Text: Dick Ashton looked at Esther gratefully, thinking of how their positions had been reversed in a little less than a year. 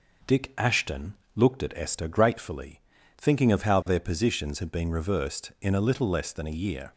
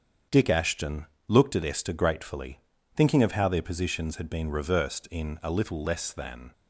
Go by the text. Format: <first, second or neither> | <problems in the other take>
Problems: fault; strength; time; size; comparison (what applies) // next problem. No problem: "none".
first | starts louder than the rest; strong; until 1.5 s; 7.5 dB // pauses between "Ashton" and "looked"; slight; at 1.0 s; 0.22 s long; slight in the first // stops before "a year"; at 6.5 s